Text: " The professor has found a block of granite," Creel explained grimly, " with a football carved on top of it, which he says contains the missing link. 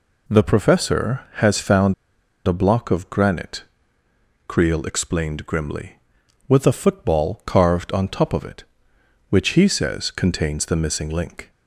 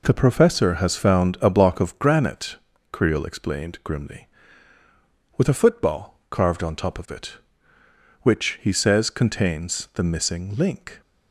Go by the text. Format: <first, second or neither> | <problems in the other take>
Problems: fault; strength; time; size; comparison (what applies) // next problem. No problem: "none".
second | pauses between "found" and "a"; noticeable; at 1.9 s; 0.52 s long